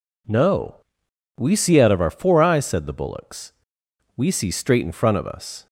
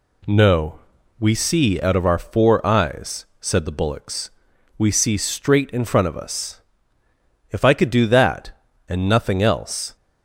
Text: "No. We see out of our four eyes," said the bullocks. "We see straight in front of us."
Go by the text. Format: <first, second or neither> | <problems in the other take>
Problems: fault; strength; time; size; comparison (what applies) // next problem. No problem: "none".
first | goes on to say "If I could do that and nothing else"; strong; from 7.4 s on; 2.4 s long